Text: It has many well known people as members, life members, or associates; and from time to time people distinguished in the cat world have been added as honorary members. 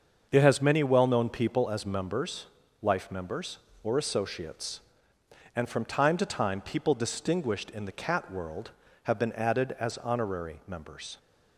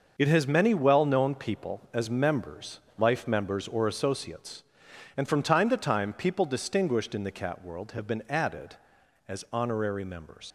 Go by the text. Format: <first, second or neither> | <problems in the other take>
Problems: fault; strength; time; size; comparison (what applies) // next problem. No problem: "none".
first | starts louder than the rest; noticeable; until 1.1 s; 6 dB; also in the first // leaves "members" unfinished; at 10.4 s; 80 ms